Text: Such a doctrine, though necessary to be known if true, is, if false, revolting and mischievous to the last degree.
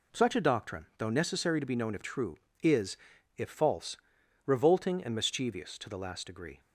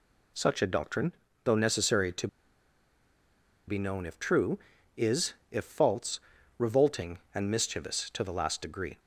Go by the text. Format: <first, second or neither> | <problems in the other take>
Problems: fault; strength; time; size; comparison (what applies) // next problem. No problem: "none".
first | pauses between "to" and "be"; strong; at 2.2 s; 1.4 s long